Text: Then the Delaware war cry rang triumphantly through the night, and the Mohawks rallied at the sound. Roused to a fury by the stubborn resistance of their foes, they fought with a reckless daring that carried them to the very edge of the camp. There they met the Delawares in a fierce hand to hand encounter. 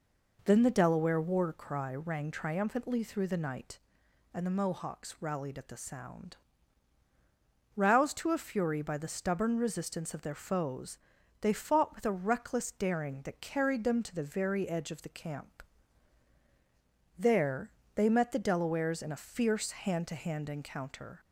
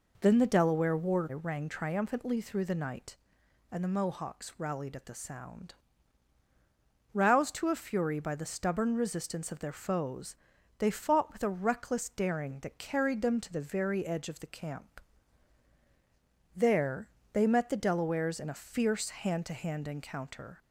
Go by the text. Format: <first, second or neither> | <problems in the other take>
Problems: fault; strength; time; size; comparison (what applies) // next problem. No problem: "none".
first | skips "cry"; at 1.2 s // pauses between "There" and "they"; slight; at 17.0 s; 0.24 s long; slight in the first